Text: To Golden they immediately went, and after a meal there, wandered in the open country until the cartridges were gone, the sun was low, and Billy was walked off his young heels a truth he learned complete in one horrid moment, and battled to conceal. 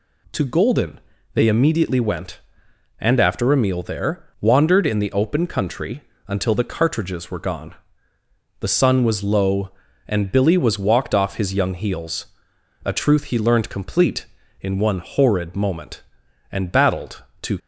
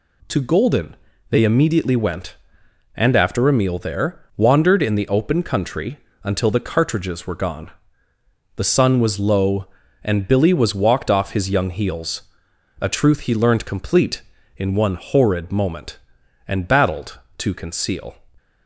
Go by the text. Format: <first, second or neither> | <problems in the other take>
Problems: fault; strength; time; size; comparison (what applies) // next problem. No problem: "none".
second | pauses between "Golden" and "they"; slight; at 0.9 s; 0.34 s long; slight in the second // pauses between "country" and "until"; slight; at 6.0 s; 0.24 s long; slight in the second // pauses between "heels" and "a"; noticeable; at 12.2 s; 0.58 s long; noticeable in the second // stops before "conceal"; at 17.5 s